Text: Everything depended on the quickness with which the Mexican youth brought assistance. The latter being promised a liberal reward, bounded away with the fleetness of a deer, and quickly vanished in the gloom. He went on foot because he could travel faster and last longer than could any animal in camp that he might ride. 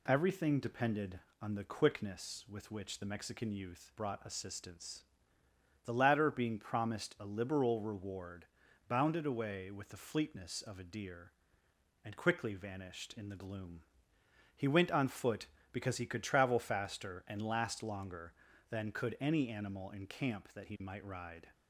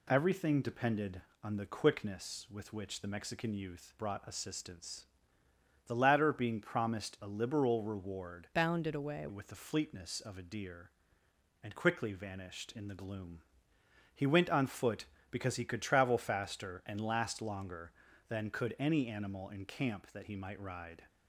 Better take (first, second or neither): first